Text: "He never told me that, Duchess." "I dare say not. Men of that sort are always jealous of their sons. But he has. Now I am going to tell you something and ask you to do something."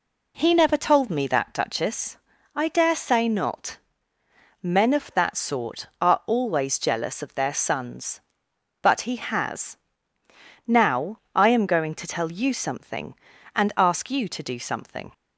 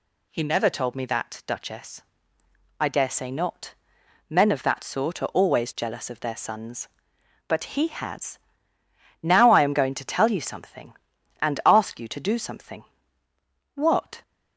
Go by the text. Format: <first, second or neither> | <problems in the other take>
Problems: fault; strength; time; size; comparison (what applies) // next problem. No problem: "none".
first | goes on to say "What"; slight; from 13.7 s on; 0.48 s long